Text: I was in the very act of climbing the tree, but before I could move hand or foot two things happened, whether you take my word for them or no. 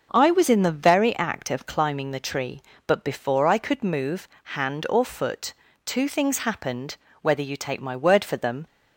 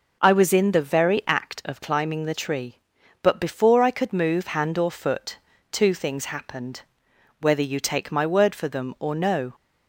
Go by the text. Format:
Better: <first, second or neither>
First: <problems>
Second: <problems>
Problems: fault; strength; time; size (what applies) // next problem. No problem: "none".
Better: second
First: starts louder than the rest; noticeable; until 1.1 s; 6 dB // pauses between "move" and "hand"; slight; at 4.2 s; 0.28 s long // pauses between "foot" and "two"; slight; at 5.5 s; 0.32 s long // stops before "or no"; at 8.6 s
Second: pauses between "foot" and "two"; slight; at 5.3 s; 0.34 s long